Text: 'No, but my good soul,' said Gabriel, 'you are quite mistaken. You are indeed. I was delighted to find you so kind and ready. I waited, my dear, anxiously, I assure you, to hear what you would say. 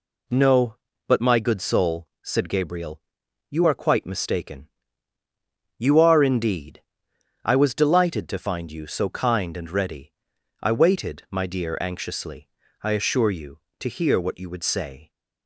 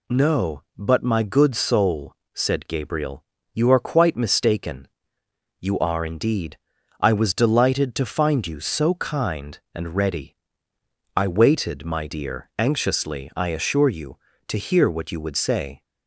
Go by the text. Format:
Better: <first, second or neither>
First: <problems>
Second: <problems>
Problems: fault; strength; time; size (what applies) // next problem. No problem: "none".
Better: neither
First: none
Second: none